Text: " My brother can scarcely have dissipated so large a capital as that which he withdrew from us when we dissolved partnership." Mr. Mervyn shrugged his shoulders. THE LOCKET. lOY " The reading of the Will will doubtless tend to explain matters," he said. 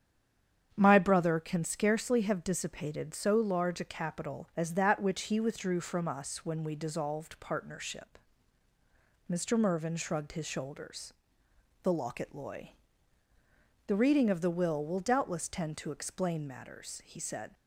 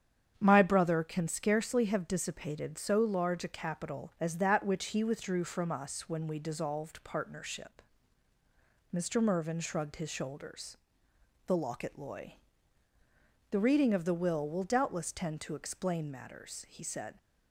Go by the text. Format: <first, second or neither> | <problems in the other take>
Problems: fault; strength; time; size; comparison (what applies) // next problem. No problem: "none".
second | stays silent before the first word; slight; until 0.7 s; 0.7 s long // starts louder than the rest; strong; until 1.7 s; 8.5 dB; strong in the second